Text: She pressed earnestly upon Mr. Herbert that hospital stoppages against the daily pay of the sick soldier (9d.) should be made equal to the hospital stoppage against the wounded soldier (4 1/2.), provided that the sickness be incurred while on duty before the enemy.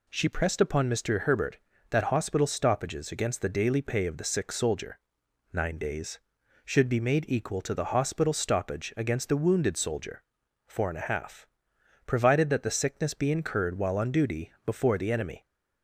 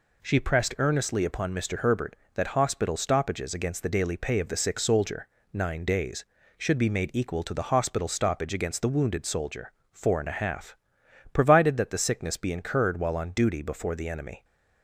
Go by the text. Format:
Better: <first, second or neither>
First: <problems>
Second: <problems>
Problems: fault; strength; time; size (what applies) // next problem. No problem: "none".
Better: second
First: skips "earnestly"; at 0.6 s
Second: none